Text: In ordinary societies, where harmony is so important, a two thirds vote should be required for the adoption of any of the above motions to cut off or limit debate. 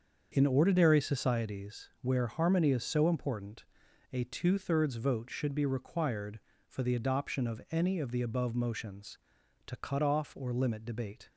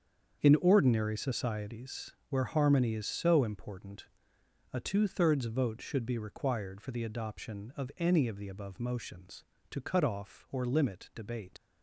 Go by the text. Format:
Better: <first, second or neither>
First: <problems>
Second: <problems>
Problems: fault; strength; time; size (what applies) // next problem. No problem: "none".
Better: first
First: starts louder than the rest; until 1.3 s; 6.5 dB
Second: starts louder than the rest; strong; until 1.4 s; 7.5 dB // leaves "debate" unfinished; at 11.5 s; 100 ms